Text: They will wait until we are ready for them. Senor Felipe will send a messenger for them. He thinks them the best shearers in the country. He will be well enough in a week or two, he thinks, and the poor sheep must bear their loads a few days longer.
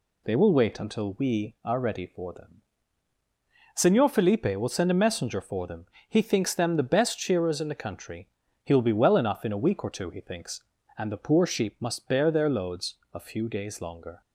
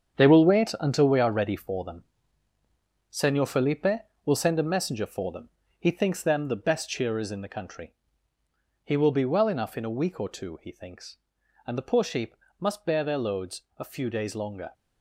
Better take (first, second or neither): first